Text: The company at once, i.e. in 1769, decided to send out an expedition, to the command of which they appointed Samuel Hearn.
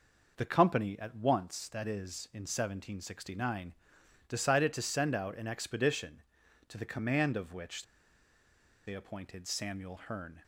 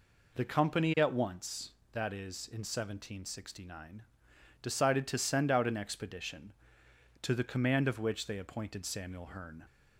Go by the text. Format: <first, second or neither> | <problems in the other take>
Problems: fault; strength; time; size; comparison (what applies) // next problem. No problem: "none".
second | pauses between "which" and "they"; at 7.8 s; 1.0 s long